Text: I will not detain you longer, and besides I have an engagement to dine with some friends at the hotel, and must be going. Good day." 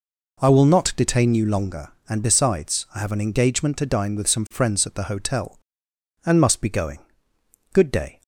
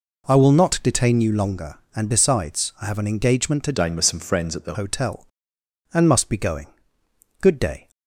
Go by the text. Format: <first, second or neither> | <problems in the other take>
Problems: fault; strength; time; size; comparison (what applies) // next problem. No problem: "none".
first | changes voice from "dine" to "the"; from 3.7 to 4.7 s; 1.0 s long